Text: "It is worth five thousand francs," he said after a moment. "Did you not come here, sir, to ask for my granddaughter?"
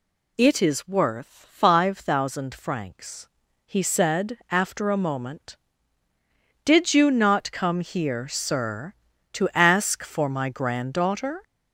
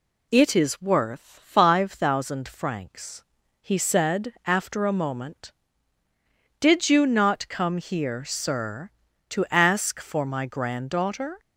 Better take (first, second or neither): second